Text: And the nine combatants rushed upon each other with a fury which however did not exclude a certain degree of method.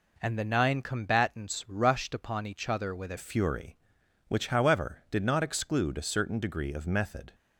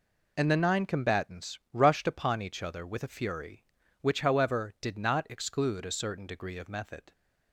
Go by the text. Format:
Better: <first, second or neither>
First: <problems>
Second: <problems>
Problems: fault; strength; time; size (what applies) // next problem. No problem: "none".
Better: second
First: changes voice at "fury"; from 3.1 s on; 4.2 s long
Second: none